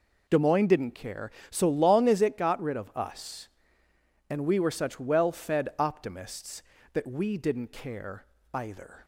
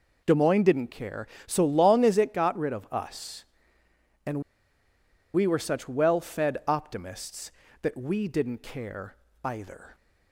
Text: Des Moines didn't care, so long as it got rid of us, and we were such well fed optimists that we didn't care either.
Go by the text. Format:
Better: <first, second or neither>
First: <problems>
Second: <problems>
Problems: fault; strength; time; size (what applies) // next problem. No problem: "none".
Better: first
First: pauses between "care" and "either"; slight; at 8.2 s; 0.28 s long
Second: pauses between "and" and "we"; noticeable; at 4.4 s; 0.92 s long // pauses between "care" and "either"; slight; at 9.1 s; 0.28 s long